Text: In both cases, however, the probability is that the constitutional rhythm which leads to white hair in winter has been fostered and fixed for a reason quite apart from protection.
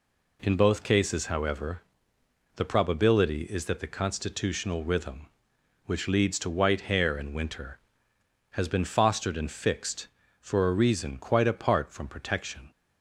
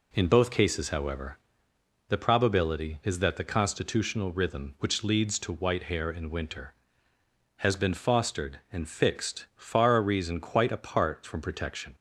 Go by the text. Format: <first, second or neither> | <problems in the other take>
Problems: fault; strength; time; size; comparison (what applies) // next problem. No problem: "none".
first | says "far" for "for"; at 9.5 s